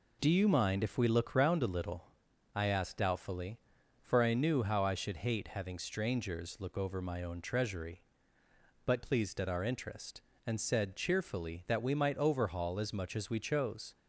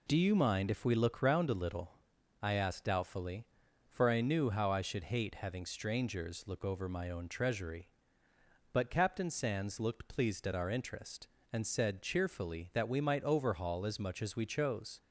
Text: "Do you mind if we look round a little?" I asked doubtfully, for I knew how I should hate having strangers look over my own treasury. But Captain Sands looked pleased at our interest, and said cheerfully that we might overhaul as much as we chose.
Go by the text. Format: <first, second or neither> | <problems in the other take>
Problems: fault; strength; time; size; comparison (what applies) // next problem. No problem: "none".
second | skips "Captain Sands looked"; at 9.0 s